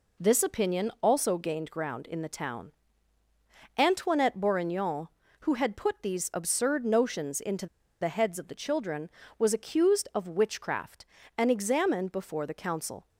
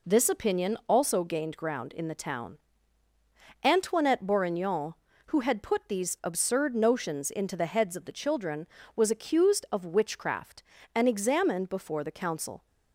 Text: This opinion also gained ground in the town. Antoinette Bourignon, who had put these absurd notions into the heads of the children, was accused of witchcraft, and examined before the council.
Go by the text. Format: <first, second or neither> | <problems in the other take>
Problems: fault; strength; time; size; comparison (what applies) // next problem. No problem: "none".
second | pauses between "into" and "the"; slight; at 7.6 s; 0.35 s long